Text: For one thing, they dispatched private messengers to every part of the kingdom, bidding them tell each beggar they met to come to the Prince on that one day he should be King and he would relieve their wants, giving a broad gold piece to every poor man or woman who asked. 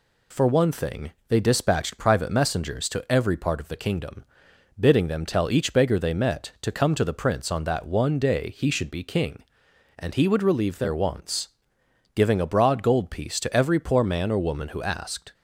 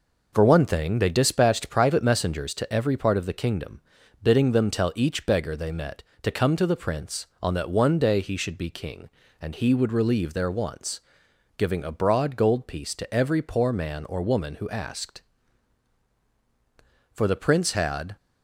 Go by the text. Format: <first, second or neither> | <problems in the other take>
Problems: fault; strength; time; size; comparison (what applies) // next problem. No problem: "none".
first | goes on to say "For the Prince had"; noticeable; from 17.1 s on; 1.0 s long